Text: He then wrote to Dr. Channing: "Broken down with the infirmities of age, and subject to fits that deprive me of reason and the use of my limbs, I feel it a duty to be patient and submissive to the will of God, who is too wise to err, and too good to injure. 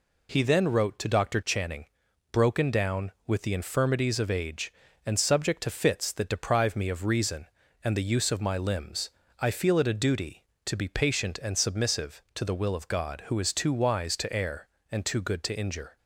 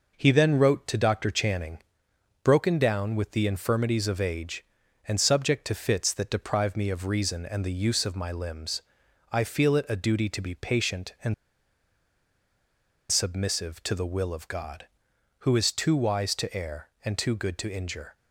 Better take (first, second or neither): first